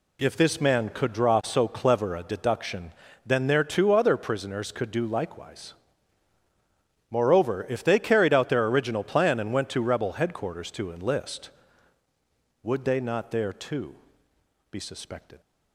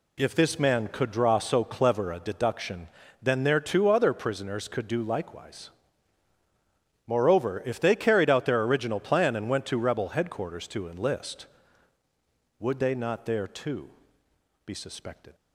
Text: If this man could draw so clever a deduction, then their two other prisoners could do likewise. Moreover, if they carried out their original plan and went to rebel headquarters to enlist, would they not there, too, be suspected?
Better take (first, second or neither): neither